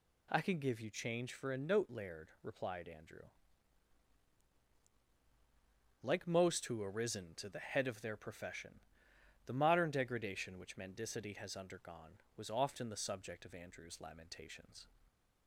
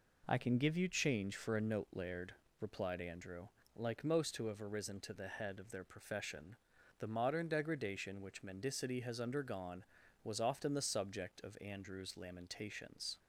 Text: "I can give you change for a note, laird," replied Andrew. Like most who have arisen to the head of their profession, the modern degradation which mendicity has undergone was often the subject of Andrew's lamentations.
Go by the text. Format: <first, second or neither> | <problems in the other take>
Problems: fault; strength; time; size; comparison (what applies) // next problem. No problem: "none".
second | skips "have"; at 6.8 s